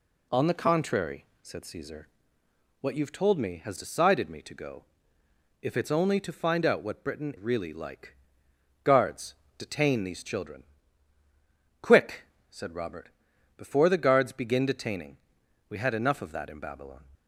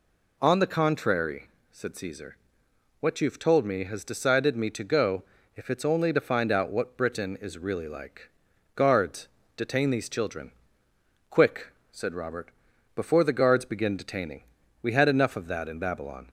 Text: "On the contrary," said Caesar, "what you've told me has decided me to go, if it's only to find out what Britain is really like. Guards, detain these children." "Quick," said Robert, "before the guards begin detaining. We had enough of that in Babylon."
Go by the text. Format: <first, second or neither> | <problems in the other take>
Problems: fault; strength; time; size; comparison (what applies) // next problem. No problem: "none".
second | skips "is"; at 7.3 s